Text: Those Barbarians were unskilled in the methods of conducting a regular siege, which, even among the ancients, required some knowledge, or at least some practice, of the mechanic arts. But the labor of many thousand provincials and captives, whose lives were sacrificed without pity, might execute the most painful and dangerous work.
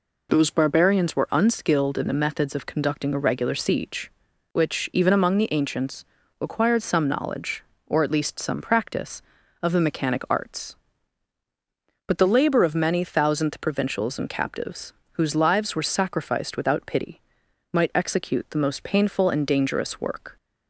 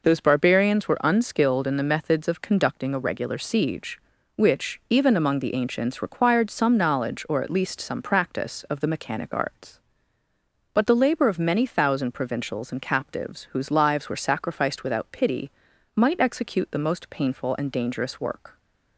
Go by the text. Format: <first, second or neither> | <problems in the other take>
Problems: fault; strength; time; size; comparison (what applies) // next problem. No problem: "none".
second | says "thousandth" for "thousand"; at 13.0 s